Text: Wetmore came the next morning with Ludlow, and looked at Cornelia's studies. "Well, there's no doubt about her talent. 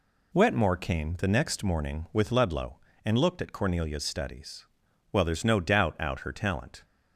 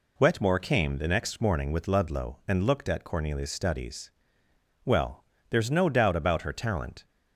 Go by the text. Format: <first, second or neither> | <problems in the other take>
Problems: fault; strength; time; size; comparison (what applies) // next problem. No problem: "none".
second | says "out" for "about"; at 5.9 s